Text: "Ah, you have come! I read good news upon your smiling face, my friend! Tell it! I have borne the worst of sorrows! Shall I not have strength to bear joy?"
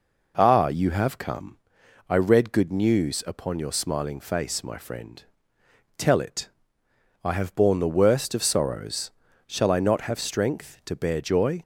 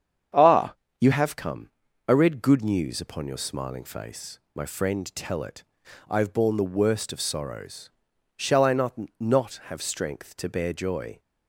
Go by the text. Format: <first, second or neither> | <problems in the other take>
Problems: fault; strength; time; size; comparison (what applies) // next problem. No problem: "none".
first | starts louder than the rest; strong; until 1.6 s; 8 dB // says "not" twice; at 9.1 s